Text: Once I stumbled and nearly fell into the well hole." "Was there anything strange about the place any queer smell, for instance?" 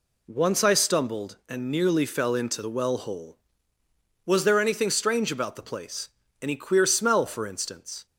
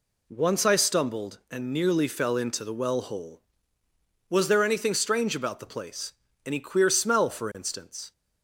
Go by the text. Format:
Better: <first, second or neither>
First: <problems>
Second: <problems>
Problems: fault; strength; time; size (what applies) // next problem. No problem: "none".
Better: neither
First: pauses between "place" and "any"; slight; at 6.0 s; 0.34 s long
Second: pauses between "place" and "any"; slight; at 6.1 s; 0.34 s long